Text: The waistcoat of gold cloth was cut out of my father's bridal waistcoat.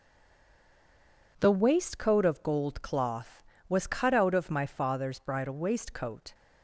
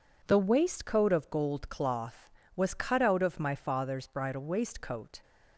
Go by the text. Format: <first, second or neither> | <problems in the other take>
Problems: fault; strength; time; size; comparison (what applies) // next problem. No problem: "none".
second | stays silent before the first word; noticeable; until 1.3 s; 1.3 s long